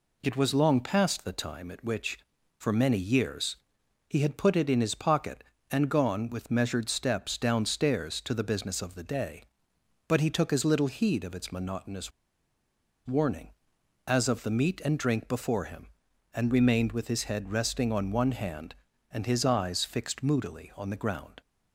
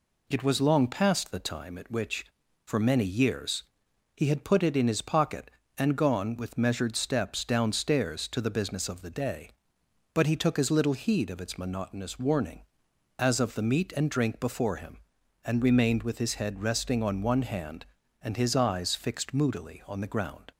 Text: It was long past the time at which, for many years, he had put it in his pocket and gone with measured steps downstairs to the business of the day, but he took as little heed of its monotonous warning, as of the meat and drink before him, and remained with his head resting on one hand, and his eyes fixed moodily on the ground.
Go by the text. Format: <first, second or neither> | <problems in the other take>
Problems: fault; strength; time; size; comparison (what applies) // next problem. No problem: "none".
second | pauses between "monotonous" and "warning"; noticeable; at 12.1 s; 0.95 s long